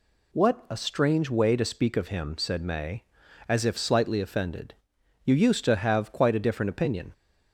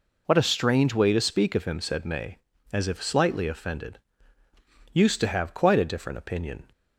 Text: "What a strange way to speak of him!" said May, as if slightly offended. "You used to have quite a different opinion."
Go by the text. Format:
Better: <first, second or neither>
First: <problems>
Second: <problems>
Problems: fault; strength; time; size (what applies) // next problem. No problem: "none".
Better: first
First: none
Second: skips "You"; at 4.4 s